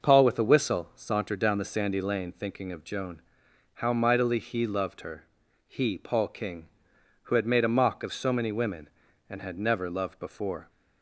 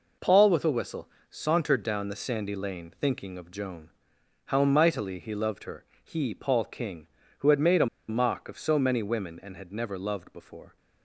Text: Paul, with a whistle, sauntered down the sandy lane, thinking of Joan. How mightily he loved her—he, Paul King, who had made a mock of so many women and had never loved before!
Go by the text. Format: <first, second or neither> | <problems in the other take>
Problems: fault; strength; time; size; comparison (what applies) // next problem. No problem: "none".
first | pauses between "a" and "mock"; slight; at 7.8 s; 0.22 s long